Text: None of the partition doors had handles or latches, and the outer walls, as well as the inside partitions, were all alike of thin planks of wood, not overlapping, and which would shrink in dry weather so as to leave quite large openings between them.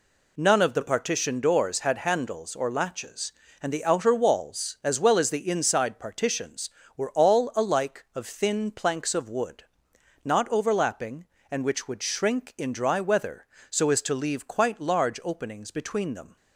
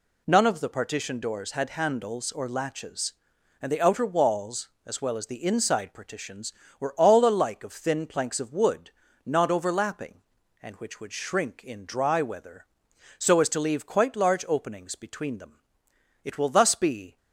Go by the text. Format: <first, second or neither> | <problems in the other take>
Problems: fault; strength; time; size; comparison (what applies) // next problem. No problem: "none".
first | goes on to say "It will thus be"; noticeable; from 16.2 s on; 0.94 s long